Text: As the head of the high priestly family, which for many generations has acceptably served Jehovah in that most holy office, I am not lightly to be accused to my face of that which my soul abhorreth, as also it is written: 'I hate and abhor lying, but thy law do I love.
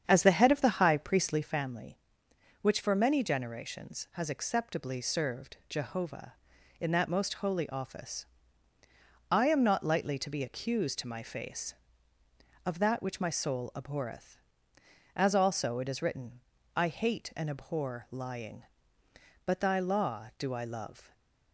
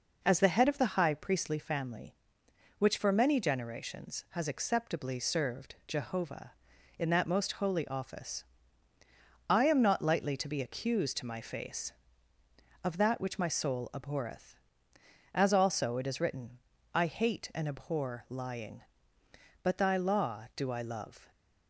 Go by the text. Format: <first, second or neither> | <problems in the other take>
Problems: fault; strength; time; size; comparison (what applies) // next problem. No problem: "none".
second | starts louder than the rest; strong; until 1.7 s; 8 dB // stays silent after the last word; slight; from 21.0 s on; 0.5 s long